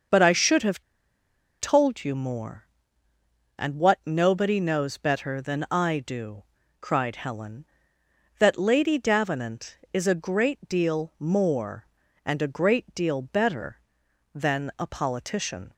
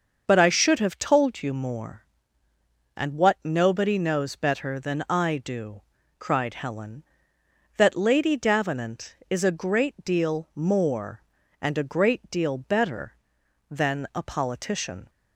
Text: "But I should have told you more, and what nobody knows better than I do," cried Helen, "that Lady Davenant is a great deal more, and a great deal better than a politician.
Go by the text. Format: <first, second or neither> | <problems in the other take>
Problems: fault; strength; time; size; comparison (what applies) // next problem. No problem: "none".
second | starts louder than the rest; until 1.9 s; 6.5 dB; also in the second // pauses between "have" and "told"; noticeable; at 0.8 s; 0.78 s long